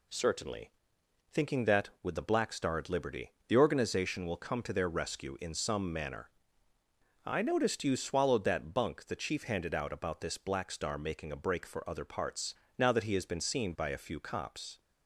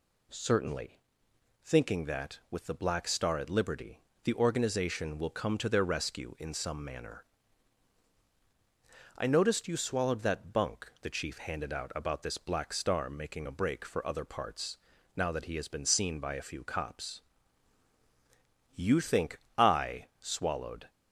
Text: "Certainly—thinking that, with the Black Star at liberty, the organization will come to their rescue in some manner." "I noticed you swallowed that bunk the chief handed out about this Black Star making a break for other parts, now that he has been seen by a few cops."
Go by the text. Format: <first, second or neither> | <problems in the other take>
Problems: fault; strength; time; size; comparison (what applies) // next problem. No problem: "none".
first | goes on to say "You think I swallowed"; strong; from 18.7 s on; 2.1 s long